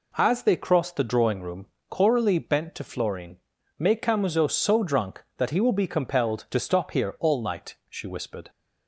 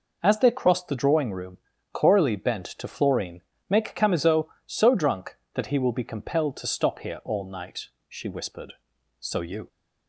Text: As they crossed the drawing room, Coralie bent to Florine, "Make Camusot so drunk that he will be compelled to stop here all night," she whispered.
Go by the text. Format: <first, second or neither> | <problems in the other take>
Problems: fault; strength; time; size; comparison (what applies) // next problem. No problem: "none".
first | goes on to say "So you"; slight; from 9.1 s on; 0.48 s long